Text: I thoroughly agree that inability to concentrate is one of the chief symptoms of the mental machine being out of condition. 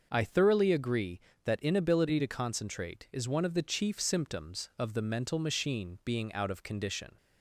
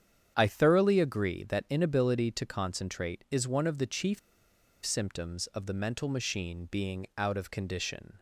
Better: first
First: starts louder than the rest; until 1.1 s; 6 dB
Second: starts louder than the rest; strong; until 1.3 s; 8.5 dB // pauses between "chief" and "symptoms"; noticeable; at 4.1 s; 0.66 s long

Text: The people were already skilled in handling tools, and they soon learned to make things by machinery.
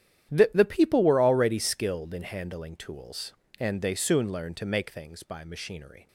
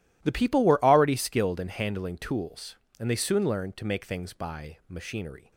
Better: second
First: starts louder than the rest; strong; until 1.3 s; 10.5 dB // says "The" twice; at 0.5 s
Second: none

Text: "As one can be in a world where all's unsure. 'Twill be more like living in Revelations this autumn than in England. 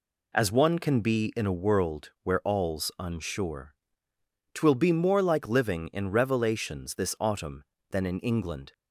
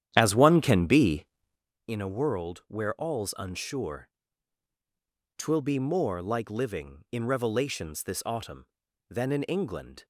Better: first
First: none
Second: starts louder than the rest; strong; until 1.7 s; 10.5 dB

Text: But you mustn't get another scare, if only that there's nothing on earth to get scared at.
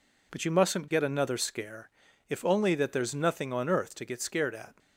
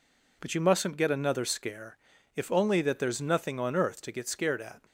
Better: neither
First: none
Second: none

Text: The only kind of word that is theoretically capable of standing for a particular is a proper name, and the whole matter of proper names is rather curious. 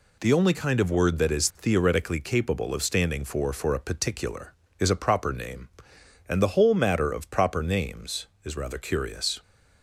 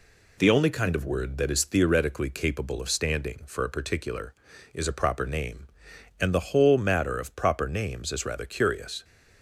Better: second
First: says "for" twice; at 3.5 s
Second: none

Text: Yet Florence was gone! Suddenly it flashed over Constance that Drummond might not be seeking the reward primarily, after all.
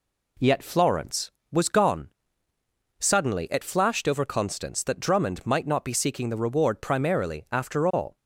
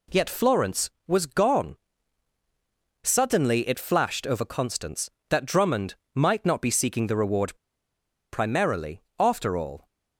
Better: first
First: none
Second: pauses between "Drummond" and "might"; slight; at 5.9 s; 0.20 s long // pauses between "reward" and "primarily"; noticeable; at 7.5 s; 0.76 s long

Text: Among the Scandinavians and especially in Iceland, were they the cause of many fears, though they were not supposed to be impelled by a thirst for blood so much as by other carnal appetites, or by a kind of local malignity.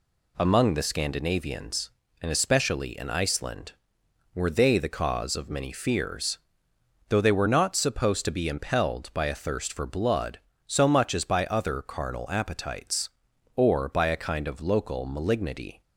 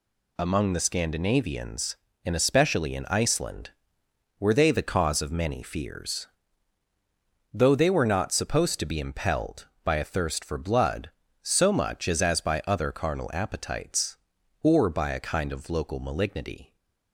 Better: first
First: none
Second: says "as" twice; at 12.2 s

